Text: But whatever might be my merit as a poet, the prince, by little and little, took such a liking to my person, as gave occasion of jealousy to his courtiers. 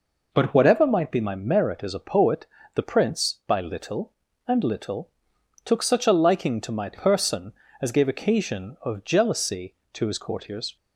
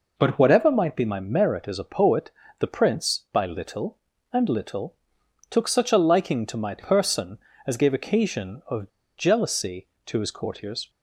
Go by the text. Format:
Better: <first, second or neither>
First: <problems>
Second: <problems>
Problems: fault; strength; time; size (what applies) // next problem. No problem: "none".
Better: first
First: none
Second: pauses between "of" and "jealousy"; slight; at 8.8 s; 0.29 s long